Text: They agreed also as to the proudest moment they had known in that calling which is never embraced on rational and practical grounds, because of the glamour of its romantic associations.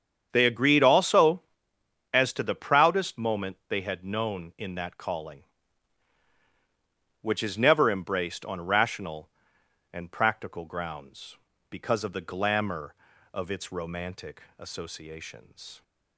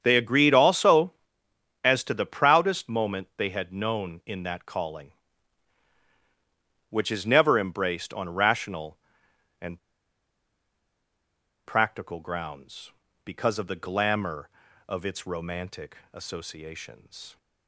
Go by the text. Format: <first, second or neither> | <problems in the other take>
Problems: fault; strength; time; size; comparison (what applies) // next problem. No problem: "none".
first | starts louder than the rest; strong; until 1.0 s; 8 dB; strong in the first // pauses between "and" and "practical"; strong; at 9.7 s; 1.8 s long // pauses between "romantic" and "associations"; slight; at 15.9 s; 0.16 s long; slight in the first